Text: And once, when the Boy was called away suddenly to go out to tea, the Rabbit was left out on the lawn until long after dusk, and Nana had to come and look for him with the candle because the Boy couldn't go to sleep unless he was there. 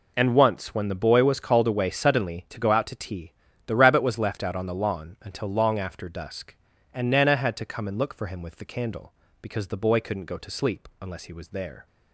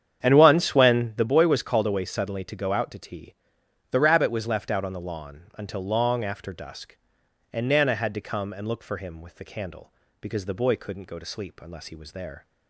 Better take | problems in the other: first | starts louder than the rest; strong; until 1.3 s; 8.5 dB

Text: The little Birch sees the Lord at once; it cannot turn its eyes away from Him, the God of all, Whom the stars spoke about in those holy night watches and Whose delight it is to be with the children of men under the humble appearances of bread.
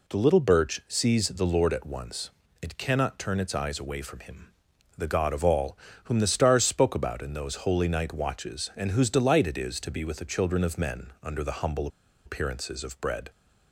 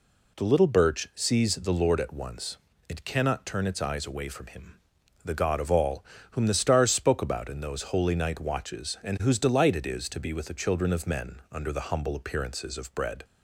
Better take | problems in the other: second | pauses between "humble" and "appearances"; at 11.8 s; 0.36 s long

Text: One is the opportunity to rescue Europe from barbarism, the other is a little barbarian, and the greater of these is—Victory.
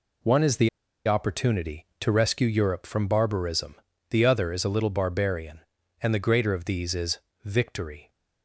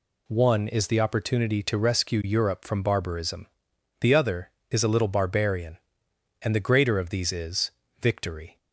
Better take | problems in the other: second | pauses between "the" and "opportunity"; at 0.6 s; 0.37 s long

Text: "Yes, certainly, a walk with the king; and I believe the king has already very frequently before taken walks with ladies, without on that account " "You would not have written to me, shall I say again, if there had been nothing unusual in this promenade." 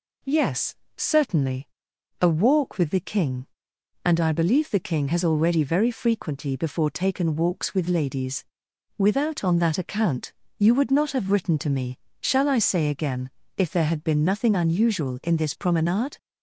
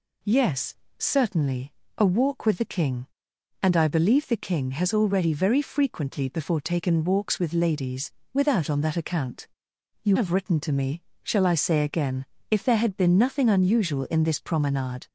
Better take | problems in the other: first | skips "would not"; at 10.1 s

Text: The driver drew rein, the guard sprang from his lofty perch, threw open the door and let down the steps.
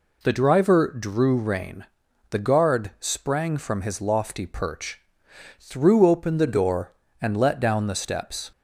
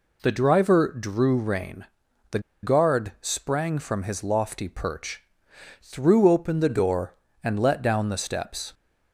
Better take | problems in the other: first | pauses between "the" and "guard"; slight; at 2.3 s; 0.23 s long

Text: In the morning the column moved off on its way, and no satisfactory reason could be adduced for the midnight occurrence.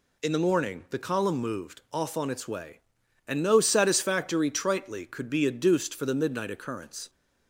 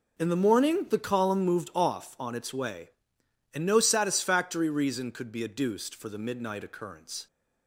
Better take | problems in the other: second | says "tritely" for "reason"; at 4.5 s

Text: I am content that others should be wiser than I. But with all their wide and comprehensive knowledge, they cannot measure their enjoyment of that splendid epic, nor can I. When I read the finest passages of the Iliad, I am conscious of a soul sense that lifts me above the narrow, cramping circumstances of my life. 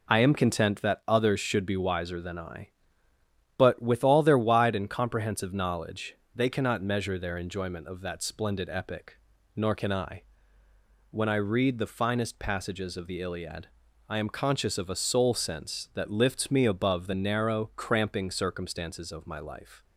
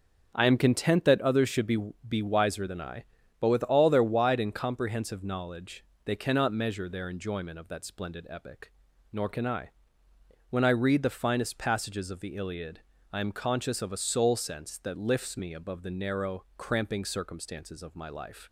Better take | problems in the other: first | starts louder than the rest; strong; until 1.3 s; 7.5 dB // says "be" twice; at 2.0 s

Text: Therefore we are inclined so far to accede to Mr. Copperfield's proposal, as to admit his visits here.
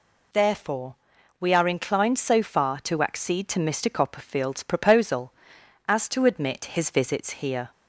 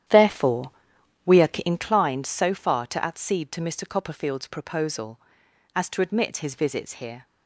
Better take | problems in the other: first | starts louder than the rest; strong; until 1.9 s; 10 dB // pauses between "Therefore" and "we"; noticeable; at 0.7 s; 0.54 s long; also in the first // pauses between "are" and "inclined"; slight; at 1.4 s; 0.16 s long

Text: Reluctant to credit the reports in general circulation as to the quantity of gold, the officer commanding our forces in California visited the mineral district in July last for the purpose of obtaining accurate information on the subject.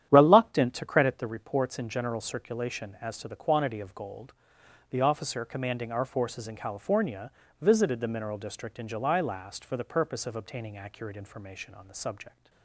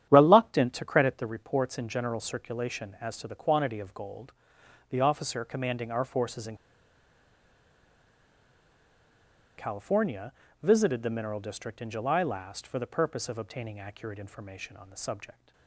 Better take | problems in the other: first | starts louder than the rest; strong; until 1.1 s; 10.5 dB; strong in the first // pauses between "in" and "California"; strong; at 6.5 s; 3.0 s long // pauses between "California" and "visited"; slight; at 10.3 s; 0.32 s long; slight in the first

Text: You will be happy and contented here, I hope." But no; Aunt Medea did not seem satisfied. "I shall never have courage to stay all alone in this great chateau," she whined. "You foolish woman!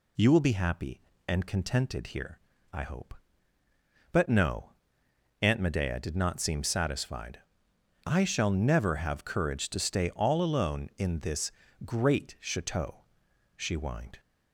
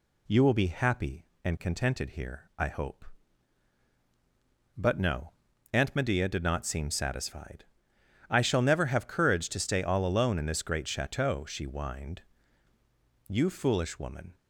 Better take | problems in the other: second | pauses between "this" and "great"; slight; at 11.5 s; 0.32 s long // stops before "You foolish woman"; at 14.1 s

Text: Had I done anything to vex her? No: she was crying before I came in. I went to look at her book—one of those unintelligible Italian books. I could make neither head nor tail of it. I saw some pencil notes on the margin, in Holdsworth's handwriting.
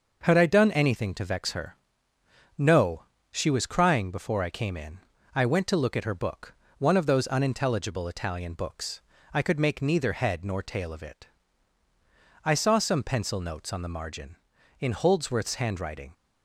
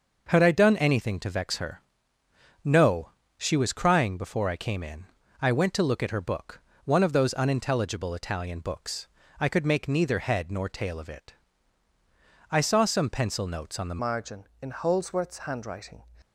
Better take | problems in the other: first | changes voice at "margin"; from 13.9 s on; 2.1 s long

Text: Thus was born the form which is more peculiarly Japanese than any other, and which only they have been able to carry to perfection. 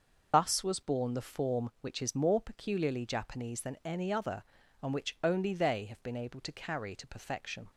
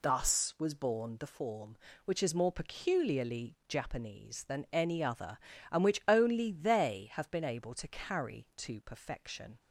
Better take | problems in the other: second | loses the start of "Thus"; at 0.3 s; 45 ms

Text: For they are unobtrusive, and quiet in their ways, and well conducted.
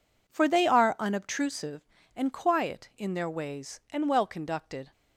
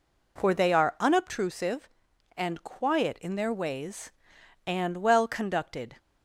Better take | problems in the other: neither | none

